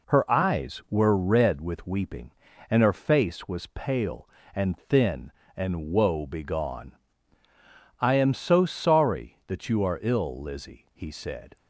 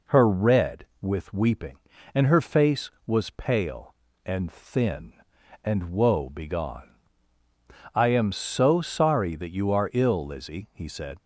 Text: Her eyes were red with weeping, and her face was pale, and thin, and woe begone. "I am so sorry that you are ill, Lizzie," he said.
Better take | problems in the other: first | skips "eyes were"; at 0.2 s

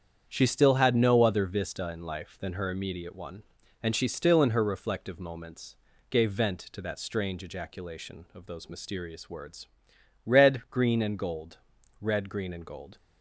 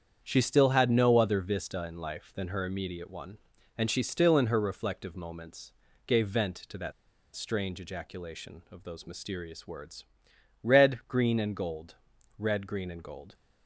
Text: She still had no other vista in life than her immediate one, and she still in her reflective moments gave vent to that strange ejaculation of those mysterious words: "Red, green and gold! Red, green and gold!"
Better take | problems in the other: first | starts louder than the rest; strong; until 1.2 s; 8 dB; strong in the first // pauses between "moments" and "gave"; slight; at 5.7 s; 0.34 s long; slight in the first // pauses between "that" and "strange"; at 6.9 s; 0.43 s long

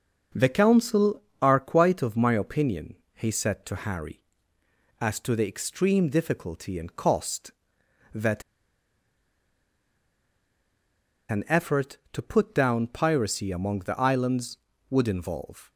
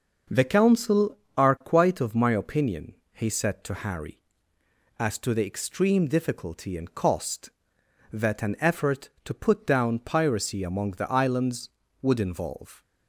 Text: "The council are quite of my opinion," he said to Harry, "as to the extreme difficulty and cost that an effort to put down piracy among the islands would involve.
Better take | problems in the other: second | starts louder than the rest; until 1.5 s; 6 dB; noticeable in the second // pauses between "that" and "an"; strong; at 8.4 s; 2.8 s long

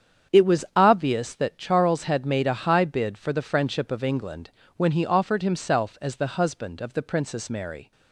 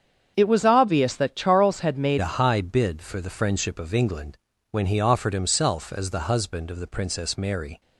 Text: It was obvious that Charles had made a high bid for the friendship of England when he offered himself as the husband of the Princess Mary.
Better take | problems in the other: first | starts louder than the rest; strong; until 1.3 s; 7.5 dB; strong in the first // changes voice at "a"; from 2.2 s on; 5.6 s long // pauses between "England" and "when"; slight; at 4.3 s; 0.36 s long; slight in the first

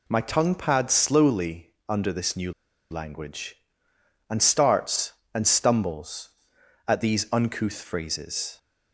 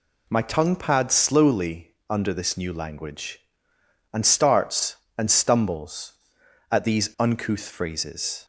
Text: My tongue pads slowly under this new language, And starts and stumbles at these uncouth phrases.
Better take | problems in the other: second | pauses between "slowly" and "under"; slight; at 1.7 s; 0.18 s long; slight in the second // pauses between "new" and "language"; at 2.5 s; 0.38 s long

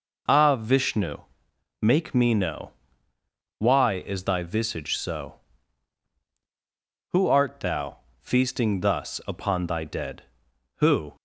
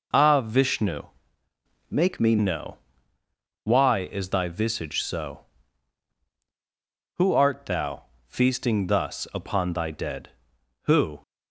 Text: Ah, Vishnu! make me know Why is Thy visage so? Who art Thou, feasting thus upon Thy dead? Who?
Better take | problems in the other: first | changes voice from "make" to "me"; from 1.9 to 2.3 s; 0.4 s long // pauses between "know" and "Why"; noticeable; at 2.7 s; 0.88 s long; noticeable in the first

